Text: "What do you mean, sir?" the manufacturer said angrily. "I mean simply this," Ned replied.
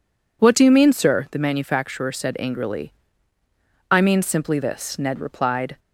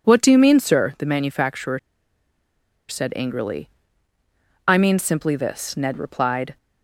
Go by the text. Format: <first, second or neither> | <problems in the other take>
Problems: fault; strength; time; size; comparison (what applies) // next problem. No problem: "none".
first | pauses between "manufacturer" and "said"; at 1.7 s; 1.0 s long